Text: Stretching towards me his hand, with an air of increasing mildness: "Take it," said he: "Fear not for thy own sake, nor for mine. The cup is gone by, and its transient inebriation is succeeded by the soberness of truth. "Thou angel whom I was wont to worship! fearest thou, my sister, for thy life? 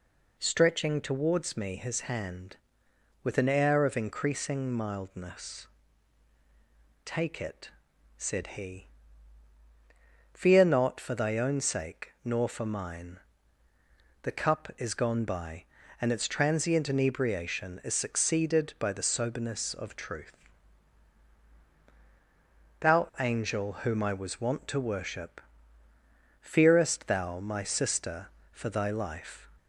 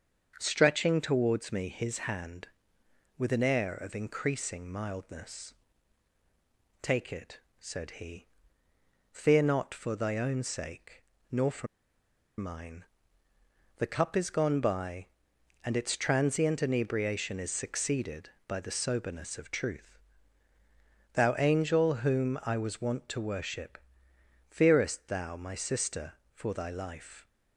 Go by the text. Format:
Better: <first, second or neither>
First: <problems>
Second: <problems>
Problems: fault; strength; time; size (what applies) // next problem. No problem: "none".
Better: first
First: none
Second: starts louder than the rest; until 1.4 s; 7 dB // pauses between "for" and "mine"; noticeable; at 11.6 s; 0.72 s long